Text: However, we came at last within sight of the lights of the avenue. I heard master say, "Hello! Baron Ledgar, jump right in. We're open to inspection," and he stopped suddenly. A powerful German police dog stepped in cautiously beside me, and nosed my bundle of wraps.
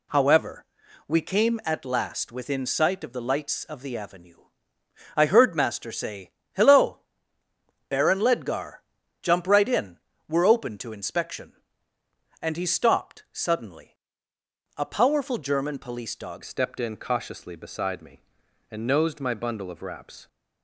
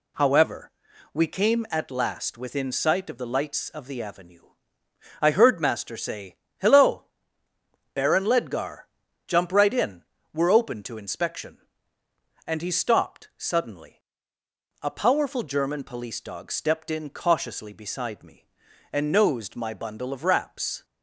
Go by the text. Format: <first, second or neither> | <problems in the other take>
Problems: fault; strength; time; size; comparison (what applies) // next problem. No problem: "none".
second | changes voice at "stepped"; from 16.4 s on; 3.8 s long